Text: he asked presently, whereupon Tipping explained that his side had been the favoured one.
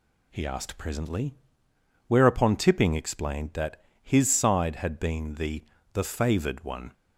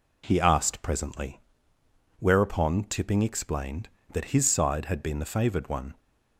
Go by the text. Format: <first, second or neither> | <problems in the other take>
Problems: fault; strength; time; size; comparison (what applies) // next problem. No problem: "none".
second | pauses between "that" and "his"; slight; at 3.8 s; 0.20 s long // says "the" twice; at 5.9 s